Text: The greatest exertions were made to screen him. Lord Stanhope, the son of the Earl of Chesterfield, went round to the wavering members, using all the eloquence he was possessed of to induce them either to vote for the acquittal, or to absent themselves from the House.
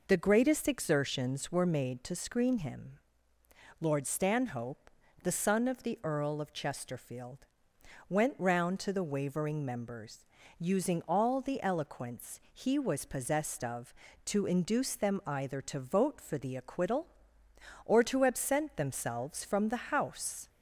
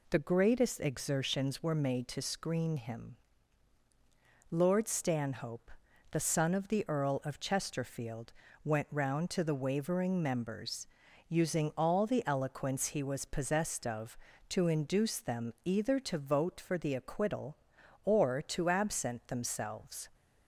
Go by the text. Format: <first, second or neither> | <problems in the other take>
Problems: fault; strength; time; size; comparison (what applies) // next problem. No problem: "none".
first | stops before "from the House"; at 20.1 s